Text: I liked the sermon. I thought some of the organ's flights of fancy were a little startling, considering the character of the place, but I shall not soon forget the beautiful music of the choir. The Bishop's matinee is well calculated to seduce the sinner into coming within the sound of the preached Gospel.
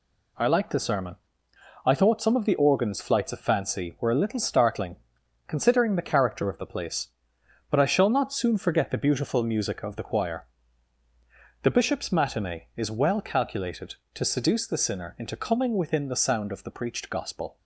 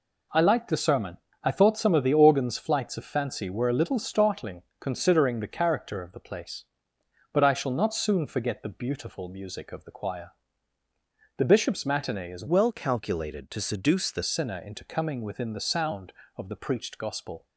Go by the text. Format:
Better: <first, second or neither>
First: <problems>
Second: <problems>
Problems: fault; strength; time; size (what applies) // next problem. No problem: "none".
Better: first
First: none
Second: changes voice from "well" to "the"; from 12.4 to 14.2 s; 1.8 s long